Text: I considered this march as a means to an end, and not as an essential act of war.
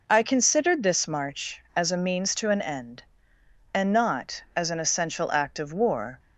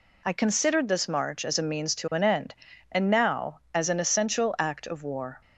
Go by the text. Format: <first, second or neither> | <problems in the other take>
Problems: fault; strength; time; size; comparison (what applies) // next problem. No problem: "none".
first | says "now" for "not"; at 3.0 s